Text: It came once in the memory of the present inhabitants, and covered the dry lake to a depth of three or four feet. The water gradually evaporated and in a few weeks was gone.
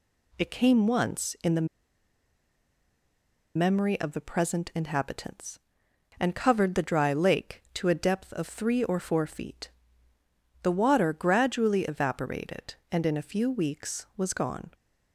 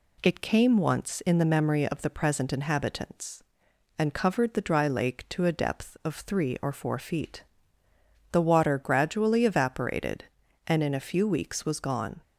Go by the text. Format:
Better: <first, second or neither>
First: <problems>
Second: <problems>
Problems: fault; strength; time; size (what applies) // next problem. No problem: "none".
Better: second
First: pauses between "the" and "memory"; strong; at 1.6 s; 1.9 s long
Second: none